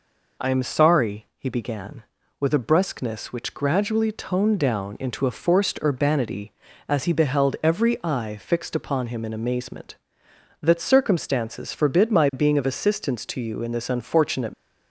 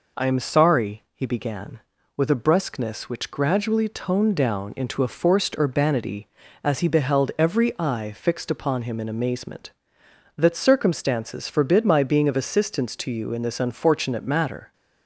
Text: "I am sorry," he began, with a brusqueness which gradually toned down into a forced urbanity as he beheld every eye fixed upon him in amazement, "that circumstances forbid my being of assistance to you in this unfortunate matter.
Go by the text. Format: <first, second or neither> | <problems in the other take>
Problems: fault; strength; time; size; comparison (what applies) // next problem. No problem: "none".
second | stops before "matter"; at 14.5 s